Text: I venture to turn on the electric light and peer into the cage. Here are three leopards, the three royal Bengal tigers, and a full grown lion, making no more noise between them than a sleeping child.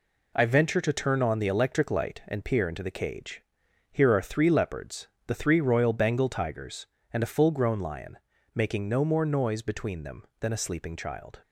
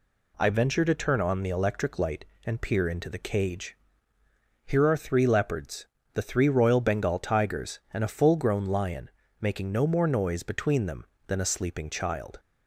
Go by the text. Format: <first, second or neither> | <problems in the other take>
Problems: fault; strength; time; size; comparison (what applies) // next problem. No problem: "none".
second | gets quieter; throughout; 6.5 dB